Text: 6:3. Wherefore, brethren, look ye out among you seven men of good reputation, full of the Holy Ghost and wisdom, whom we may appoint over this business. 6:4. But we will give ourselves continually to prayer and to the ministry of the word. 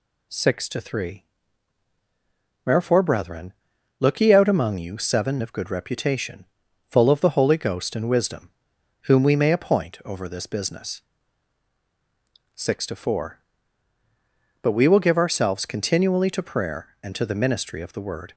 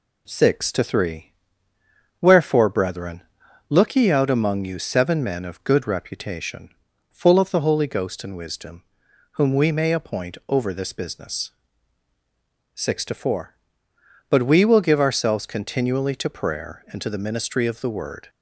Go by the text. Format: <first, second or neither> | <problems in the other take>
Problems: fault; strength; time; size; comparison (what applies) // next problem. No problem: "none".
second | skips "men"; at 5.4 s